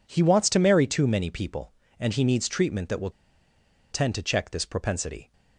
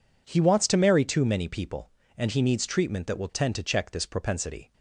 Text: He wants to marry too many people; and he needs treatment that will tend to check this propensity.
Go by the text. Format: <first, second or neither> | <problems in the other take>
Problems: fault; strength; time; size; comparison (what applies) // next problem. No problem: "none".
second | pauses between "will" and "tend"; noticeable; at 3.1 s; 0.81 s long